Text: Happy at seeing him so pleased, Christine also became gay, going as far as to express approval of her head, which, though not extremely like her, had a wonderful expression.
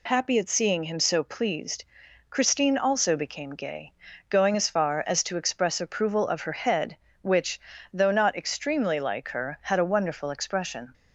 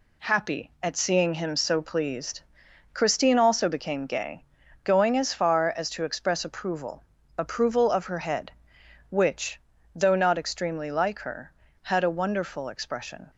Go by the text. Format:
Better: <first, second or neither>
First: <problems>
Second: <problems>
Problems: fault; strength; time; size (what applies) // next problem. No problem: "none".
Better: first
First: none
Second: says "approval" twice; at 7.3 s